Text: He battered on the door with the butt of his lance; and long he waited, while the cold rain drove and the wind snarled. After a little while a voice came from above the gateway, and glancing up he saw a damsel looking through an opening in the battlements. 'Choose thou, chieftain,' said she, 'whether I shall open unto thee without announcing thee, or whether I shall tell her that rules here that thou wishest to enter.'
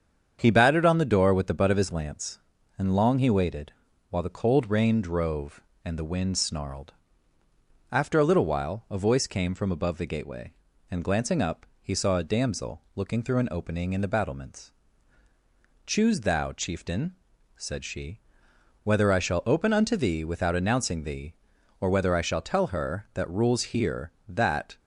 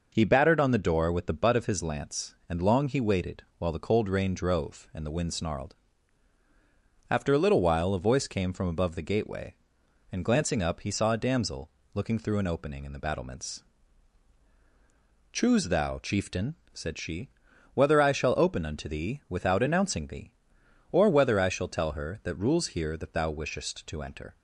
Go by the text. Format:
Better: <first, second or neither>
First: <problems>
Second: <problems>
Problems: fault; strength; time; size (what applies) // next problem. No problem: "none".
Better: second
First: starts louder than the rest; strong; until 1.4 s; 7.5 dB // pauses between "up" and "he"; slight; at 11.6 s; 0.16 s long // pauses between "damsel" and "looking"; slight; at 12.7 s; 0.16 s long // stops before "thou wishest to enter"; at 24.7 s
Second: pauses between "damsel" and "looking"; slight; at 11.7 s; 0.24 s long